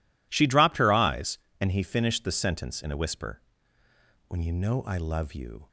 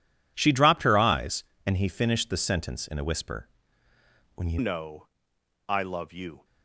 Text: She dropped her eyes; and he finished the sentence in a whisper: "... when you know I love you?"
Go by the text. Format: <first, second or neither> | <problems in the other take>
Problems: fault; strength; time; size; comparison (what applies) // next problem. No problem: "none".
first | changes voice at "know"; from 4.5 s on; 1.9 s long // pauses between "know" and "I"; noticeable; at 5.0 s; 0.58 s long